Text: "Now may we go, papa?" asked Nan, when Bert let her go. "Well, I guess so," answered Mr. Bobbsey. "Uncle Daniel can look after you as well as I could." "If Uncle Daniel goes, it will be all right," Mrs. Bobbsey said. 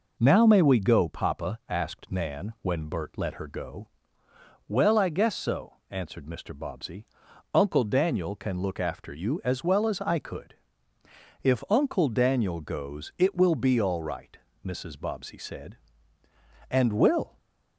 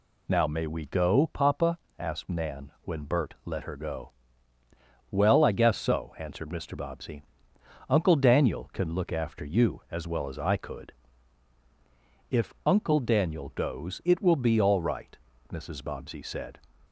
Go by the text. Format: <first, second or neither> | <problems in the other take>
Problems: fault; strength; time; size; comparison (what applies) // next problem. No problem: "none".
second | goes on to say "And will"; noticeable; from 16.7 s on; 0.66 s long